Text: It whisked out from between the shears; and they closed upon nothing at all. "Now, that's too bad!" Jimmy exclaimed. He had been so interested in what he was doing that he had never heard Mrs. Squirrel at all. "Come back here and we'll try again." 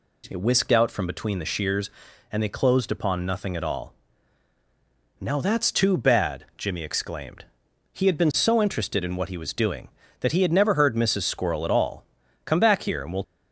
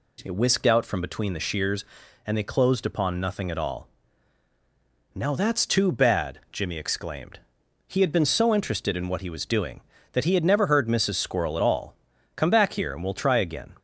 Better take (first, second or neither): second